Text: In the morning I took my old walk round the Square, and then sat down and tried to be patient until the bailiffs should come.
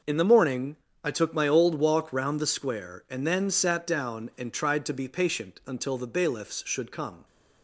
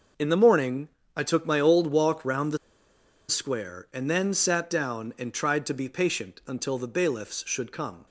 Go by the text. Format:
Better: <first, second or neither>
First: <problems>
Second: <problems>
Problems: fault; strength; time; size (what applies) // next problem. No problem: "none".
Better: first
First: pauses between "morning" and "I"; slight; at 0.7 s; 0.30 s long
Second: pauses between "morning" and "I"; slight; at 0.8 s; 0.30 s long // pauses between "the" and "Square"; noticeable; at 2.5 s; 0.72 s long